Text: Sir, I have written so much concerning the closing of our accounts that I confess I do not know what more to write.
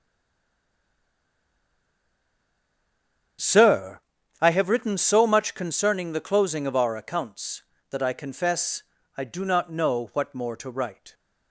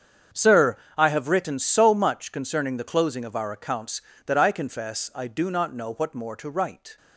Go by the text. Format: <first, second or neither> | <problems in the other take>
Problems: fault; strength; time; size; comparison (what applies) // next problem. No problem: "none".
second | stays silent before the first word; strong; until 3.3 s; 3.3 s long // starts louder than the rest; strong; until 4.8 s; 8 dB; strong in the second // pauses between "confess" and "I"; slight; at 8.8 s; 0.34 s long